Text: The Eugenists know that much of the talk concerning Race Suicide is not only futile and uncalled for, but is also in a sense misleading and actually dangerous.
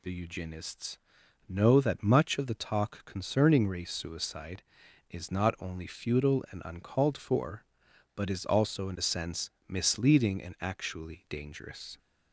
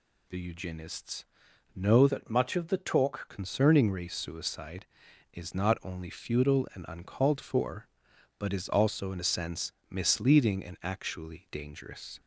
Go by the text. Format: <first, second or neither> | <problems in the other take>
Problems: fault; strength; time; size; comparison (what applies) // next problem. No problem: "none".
first | pauses between "Eugenists" and "know"; noticeable; at 1.2 s; 0.50 s long; noticeable in the first // changes voice from "that" to "talk"; from 2.0 to 3.2 s; 1.2 s long // pauses between "sense" and "misleading"; slight; at 9.7 s; 0.18 s long; slight in the first